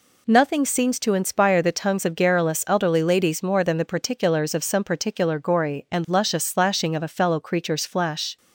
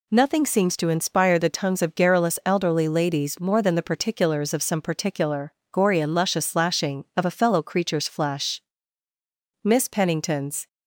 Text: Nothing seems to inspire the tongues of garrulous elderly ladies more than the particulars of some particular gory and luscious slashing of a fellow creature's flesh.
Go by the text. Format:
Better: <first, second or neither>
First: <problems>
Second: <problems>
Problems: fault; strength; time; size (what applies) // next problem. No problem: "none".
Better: first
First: none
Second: pauses between "particular" and "gory"; slight; at 5.5 s; 0.20 s long // goes on to say "Miss Pennington's"; noticeable; from 9.6 s on; 1.0 s long